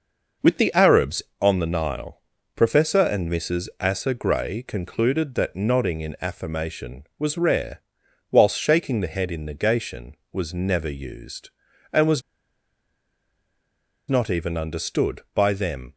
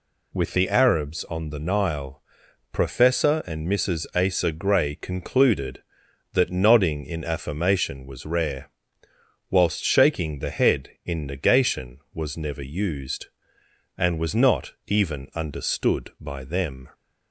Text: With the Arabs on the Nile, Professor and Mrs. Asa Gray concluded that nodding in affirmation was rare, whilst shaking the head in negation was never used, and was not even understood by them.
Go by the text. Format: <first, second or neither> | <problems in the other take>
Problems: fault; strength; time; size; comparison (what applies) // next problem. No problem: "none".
second | pauses between "was" and "not"; strong; at 12.2 s; 1.8 s long